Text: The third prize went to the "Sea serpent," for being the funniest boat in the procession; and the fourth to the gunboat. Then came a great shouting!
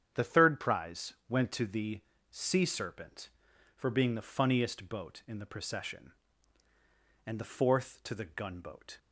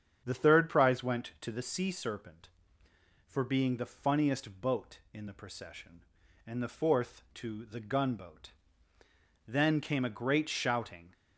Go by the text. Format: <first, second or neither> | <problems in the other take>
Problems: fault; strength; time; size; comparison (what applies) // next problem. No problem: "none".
second | starts louder than the rest; strong; until 1.3 s; 8.5 dB; strong in the second // pauses between "prize" and "went"; slight; at 1.1 s; 0.16 s long // pauses between "the" and "Sea"; slight; at 1.9 s; 0.32 s long // stops before "Then came a great shouting"; at 8.9 s